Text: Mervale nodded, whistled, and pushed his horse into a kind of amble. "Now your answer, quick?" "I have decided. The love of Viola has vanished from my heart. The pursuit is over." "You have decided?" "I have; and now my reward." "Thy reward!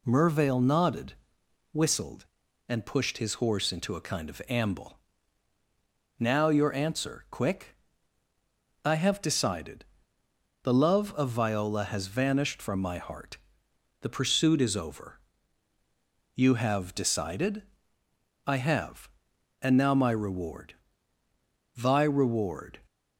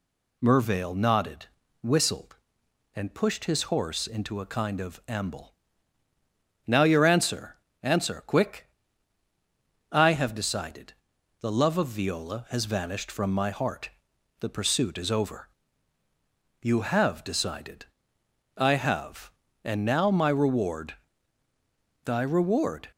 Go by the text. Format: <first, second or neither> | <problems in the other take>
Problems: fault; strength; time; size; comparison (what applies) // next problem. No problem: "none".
first | says "answer" twice; at 7.8 s